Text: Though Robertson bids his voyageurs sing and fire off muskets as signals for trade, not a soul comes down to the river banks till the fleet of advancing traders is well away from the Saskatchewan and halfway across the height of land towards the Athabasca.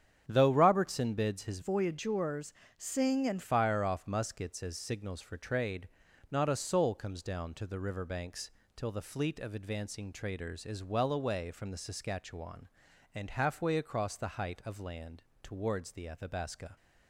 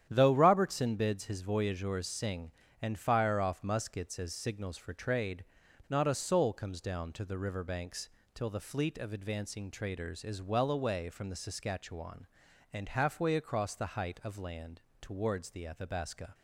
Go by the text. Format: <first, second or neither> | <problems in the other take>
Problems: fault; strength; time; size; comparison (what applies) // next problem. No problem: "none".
second | starts louder than the rest; strong; until 1.2 s; 8.5 dB; strong in the second // changes voice from "voyageurs" to "and"; from 1.6 to 3.4 s; 1.8 s long // pauses between "voyageurs" and "sing"; slight; at 2.5 s; 0.24 s long // pauses between "banks" and "till"; slight; at 8.4 s; 0.26 s long; slight in the second // pauses between "land" and "towards"; slight; at 15.2 s; 0.18 s long; slight in the second